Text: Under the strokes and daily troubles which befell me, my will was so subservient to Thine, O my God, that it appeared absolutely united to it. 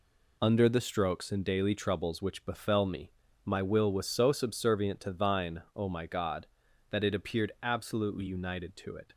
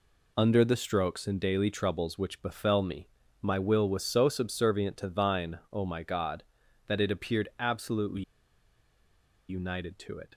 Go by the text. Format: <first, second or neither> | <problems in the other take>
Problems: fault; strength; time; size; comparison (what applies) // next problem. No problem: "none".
first | pauses between "absolutely" and "united"; strong; at 8.2 s; 1.2 s long